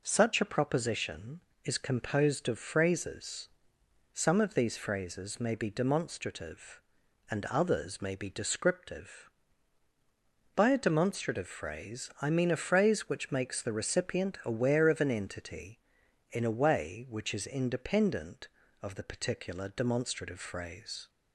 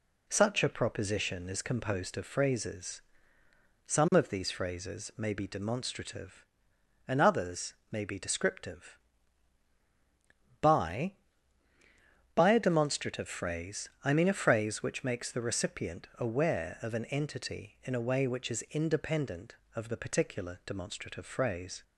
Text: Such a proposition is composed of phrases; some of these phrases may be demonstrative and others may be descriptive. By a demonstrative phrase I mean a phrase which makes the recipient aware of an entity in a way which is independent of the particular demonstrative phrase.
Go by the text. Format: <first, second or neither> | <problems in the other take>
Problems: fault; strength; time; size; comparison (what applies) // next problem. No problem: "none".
first | pauses between "others" and "may"; slight; at 7.7 s; 0.18 s long // says "By" twice; at 12.3 s // pauses between "phrase" and "I"; slight; at 13.8 s; 0.16 s long